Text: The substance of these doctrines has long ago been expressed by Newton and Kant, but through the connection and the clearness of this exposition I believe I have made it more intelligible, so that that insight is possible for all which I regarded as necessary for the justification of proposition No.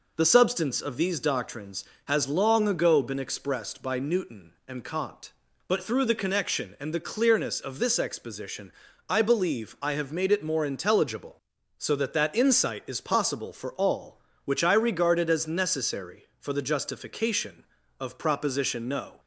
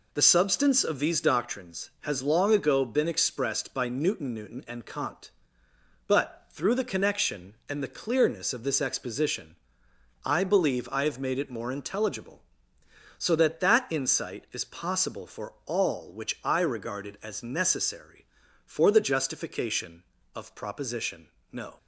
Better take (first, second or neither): first